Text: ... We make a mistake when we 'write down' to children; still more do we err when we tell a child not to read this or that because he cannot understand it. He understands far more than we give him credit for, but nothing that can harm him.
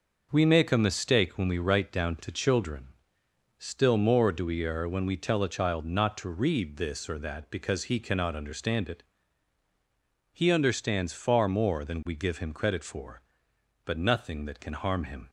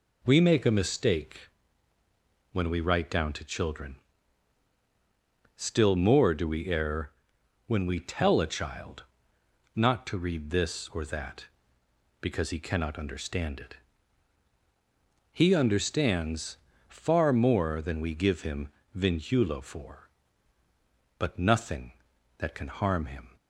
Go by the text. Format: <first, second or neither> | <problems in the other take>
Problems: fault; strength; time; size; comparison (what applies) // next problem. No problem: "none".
first | pauses between "mistake" and "when"; at 1.4 s; 1.0 s long // pauses between "err" and "when"; noticeable; at 7.1 s; 0.56 s long // pauses between "child" and "not"; noticeable; at 9.0 s; 0.72 s long // pauses between "understands" and "far"; slight; at 16.5 s; 0.32 s long // says "vinculo" for "credit"; at 18.9 s